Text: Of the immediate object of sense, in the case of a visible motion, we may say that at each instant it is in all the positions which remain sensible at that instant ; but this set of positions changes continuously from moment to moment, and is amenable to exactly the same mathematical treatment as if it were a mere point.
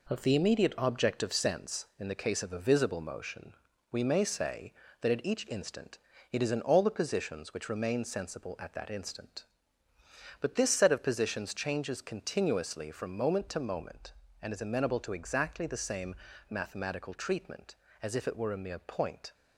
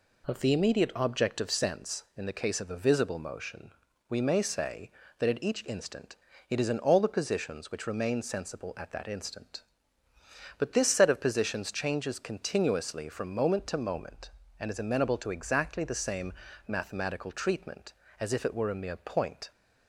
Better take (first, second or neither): second